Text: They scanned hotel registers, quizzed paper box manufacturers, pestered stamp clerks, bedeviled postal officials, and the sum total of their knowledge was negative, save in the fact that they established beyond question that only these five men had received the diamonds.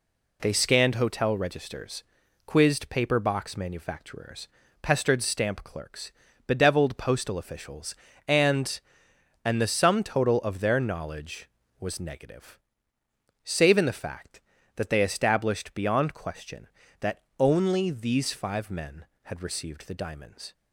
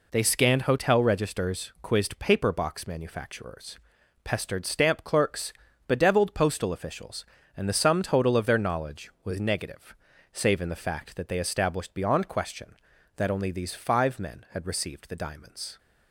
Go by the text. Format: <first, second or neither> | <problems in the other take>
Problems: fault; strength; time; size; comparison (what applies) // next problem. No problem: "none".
second | says "and" twice; at 9.4 s // pauses between "that" and "only"; slight; at 17.2 s; 0.18 s long